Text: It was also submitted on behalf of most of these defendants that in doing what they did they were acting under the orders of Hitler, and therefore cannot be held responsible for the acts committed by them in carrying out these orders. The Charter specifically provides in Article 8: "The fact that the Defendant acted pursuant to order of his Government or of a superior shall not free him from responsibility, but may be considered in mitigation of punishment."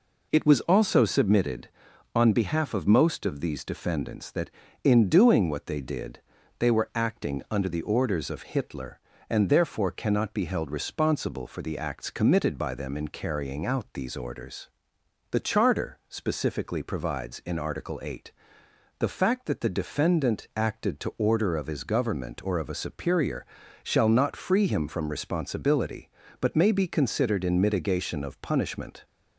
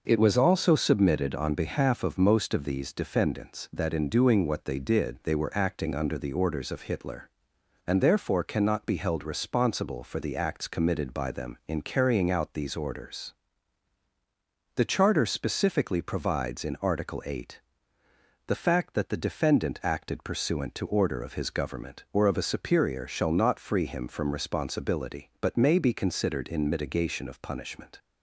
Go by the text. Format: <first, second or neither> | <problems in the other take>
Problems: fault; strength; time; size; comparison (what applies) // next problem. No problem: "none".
second | pauses between "did" and "they"; at 6.1 s; 0.40 s long // skips "pursuant"; at 20.9 s // pauses between "superior" and "shall"; slight; at 23.4 s; 0.36 s long